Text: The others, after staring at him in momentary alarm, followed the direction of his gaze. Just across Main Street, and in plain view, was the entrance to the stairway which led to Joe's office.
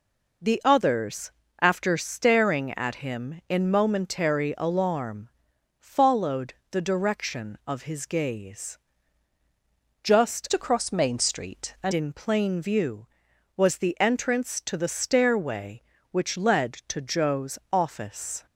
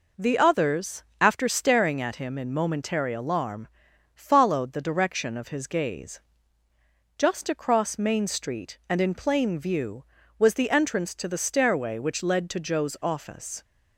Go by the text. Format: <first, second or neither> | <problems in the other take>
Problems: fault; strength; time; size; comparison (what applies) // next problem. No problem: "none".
second | pauses between "followed" and "the"; slight; at 6.5 s; 0.18 s long // changes voice from "across" to "and"; from 10.5 to 11.9 s; 1.4 s long